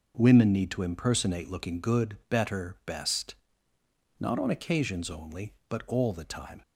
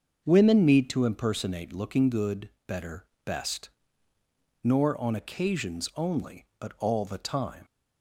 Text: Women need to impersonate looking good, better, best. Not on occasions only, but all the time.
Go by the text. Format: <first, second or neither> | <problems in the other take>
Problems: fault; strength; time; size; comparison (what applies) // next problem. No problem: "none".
first | starts louder than the rest; until 1.2 s; 6.5 dB // says "Nor" for "Not"; at 4.6 s